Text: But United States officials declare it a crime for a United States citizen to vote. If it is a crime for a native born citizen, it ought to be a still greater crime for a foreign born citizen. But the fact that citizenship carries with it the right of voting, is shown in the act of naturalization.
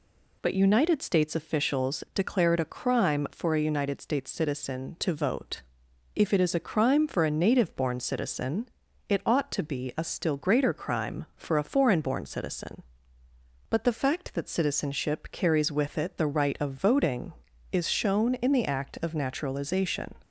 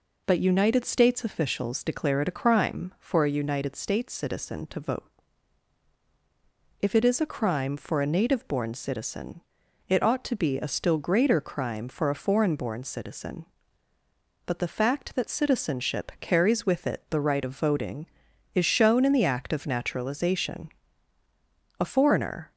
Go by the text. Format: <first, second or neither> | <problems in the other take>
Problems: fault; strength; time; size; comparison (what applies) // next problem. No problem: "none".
first | goes on to say "A foreigner"; noticeable; from 21.7 s on; 0.72 s long